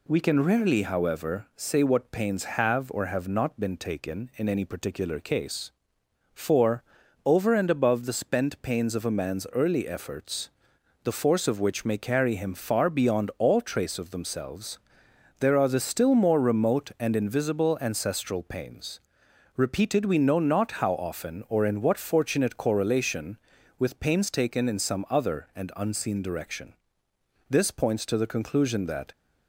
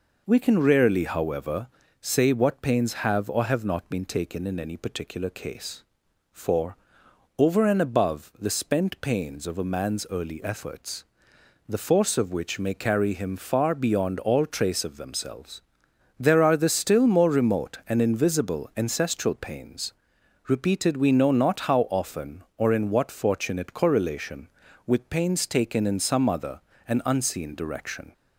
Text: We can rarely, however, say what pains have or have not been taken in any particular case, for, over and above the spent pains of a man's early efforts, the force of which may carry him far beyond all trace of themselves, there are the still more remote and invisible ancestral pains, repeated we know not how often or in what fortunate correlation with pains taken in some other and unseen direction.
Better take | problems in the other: second | goes on to say "This points to the conclusion that"; from 27.4 s on; 1.6 s long

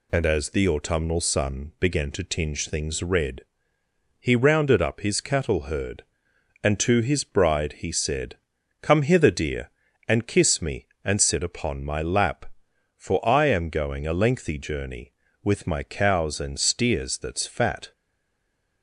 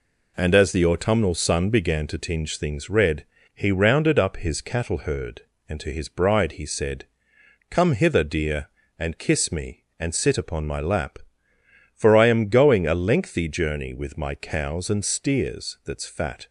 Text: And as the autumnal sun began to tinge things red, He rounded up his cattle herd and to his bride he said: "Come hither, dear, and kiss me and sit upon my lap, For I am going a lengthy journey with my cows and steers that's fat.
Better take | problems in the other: second | stays silent after the last word; slight; from 17.9 s on; 0.9 s long

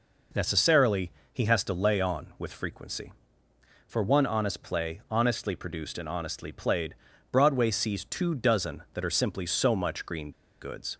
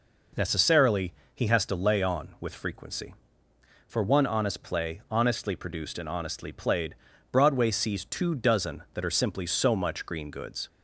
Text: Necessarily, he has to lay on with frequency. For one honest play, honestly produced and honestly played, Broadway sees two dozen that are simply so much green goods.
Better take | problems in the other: second | pauses between "green" and "goods"; slight; at 10.3 s; 0.31 s long

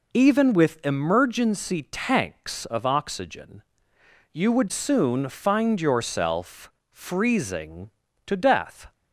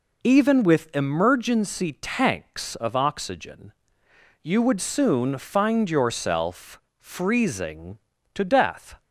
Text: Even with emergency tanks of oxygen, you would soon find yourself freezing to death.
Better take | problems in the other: neither | pauses between "yourself" and "freezing"; slight; the same in both

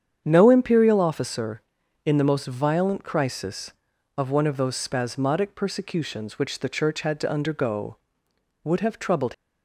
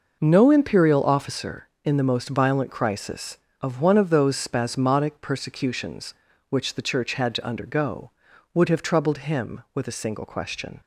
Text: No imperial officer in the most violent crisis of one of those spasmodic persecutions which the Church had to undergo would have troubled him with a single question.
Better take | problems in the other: second | starts louder than the rest; strong; until 1.2 s; 8.5 dB // stops before "him with a single question"; at 9.3 s

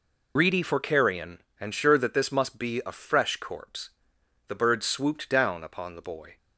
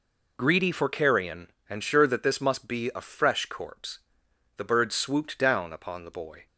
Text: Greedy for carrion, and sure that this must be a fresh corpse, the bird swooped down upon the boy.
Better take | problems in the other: second | loses the start of "Greedy"; at 0.3 s; 65 ms

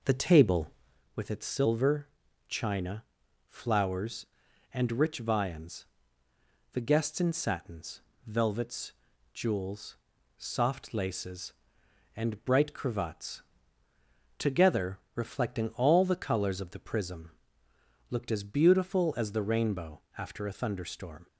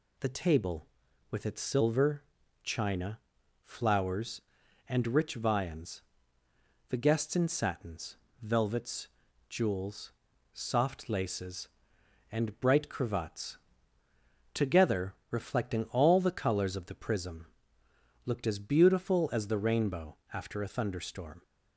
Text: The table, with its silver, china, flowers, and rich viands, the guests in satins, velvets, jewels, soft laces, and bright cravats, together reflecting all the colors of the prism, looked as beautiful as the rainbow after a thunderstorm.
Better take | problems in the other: second | starts louder than the rest; noticeable; until 1.1 s; 5 dB // pauses between "together" and "reflecting"; slight; at 14.9 s; 0.18 s long; slight in the second // pauses between "rainbow" and "after"; slight; at 20.0 s; 0.16 s long; slight in the second

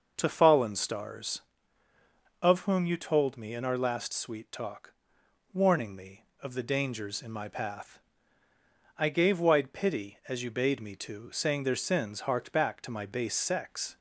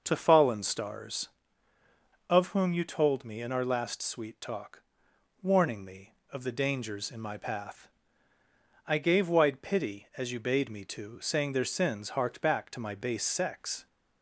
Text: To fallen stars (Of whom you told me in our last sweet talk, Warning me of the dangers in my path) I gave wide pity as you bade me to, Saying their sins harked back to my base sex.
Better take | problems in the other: neither | starts louder than the rest; noticeable; the same in both

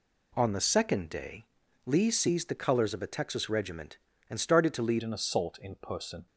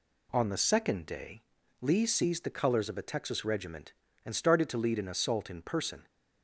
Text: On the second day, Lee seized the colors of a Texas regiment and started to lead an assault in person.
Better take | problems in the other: second | changes voice at "an"; from 5.0 s on; 1.2 s long

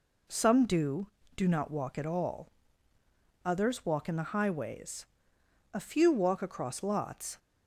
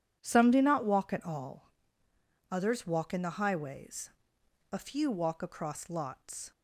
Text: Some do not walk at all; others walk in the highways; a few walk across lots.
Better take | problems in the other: second | says "do" twice; at 1.3 s

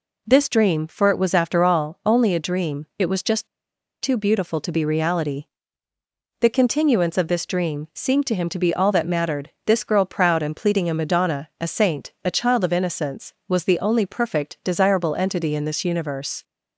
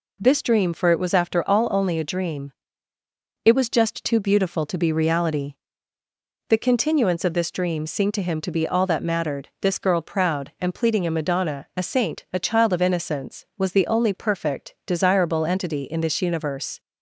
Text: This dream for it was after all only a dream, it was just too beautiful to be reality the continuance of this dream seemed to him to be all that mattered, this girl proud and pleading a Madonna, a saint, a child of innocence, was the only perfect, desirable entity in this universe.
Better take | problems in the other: second | pauses between "just" and "too"; noticeable; at 3.4 s; 0.54 s long // pauses between "reality" and "the"; noticeable; at 5.4 s; 0.94 s long; noticeable in the second

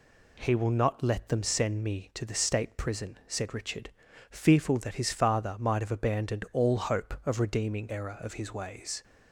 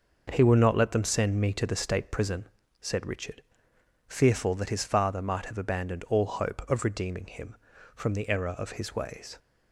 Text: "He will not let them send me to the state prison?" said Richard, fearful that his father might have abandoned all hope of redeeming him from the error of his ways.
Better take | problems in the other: second | skips "him from the"; at 7.8 s

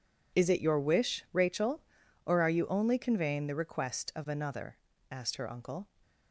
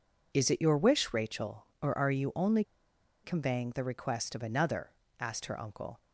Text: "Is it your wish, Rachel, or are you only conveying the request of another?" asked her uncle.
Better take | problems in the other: first | pauses between "only" and "conveying"; noticeable; at 2.6 s; 0.59 s long

